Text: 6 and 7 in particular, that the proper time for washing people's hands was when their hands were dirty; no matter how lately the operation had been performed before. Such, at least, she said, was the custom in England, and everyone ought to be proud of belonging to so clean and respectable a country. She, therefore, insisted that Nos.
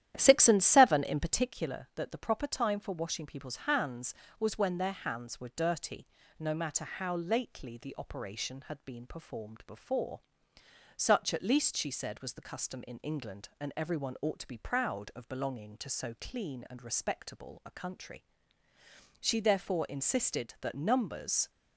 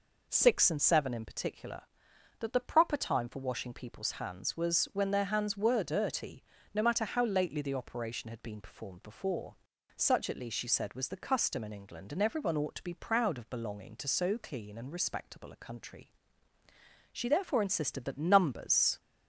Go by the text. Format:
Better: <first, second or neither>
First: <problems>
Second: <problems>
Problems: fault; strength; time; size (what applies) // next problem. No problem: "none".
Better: second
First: starts louder than the rest; strong; until 1.5 s; 11.5 dB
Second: none